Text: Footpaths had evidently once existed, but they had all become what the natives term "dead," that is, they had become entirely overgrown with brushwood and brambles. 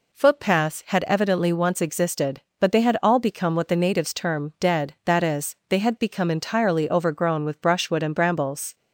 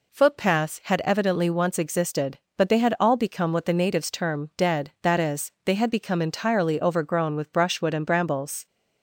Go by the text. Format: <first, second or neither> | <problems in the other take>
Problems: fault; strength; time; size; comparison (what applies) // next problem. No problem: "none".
neither | none